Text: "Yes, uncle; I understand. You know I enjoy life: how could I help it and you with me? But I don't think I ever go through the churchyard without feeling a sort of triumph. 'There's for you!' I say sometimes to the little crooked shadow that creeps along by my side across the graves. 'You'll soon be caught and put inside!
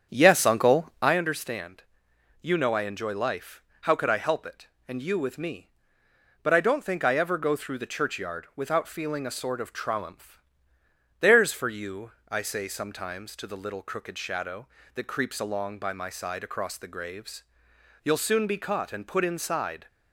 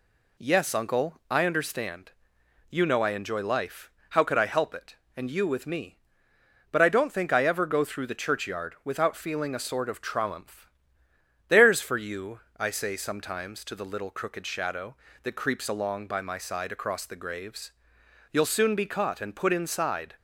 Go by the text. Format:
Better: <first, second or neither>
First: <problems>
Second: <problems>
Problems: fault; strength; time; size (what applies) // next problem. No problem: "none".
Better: second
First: starts louder than the rest; strong; until 1.2 s; 8 dB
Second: none